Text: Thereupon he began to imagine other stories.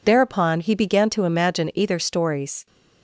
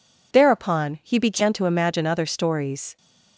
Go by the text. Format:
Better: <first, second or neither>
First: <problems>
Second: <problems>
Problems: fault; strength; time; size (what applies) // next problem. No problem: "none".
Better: second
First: says "either" for "other"; at 1.7 s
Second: none